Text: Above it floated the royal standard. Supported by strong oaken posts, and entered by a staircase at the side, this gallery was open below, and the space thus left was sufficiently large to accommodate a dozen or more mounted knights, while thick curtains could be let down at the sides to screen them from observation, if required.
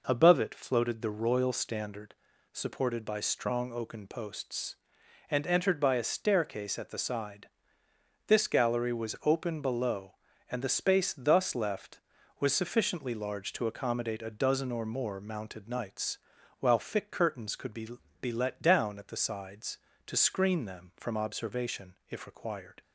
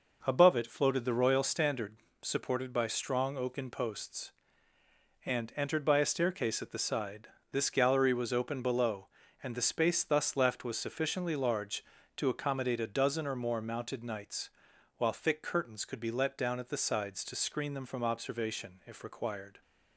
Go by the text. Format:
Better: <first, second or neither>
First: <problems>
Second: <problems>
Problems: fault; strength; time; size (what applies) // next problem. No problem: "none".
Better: second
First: says "be" twice; at 18.2 s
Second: none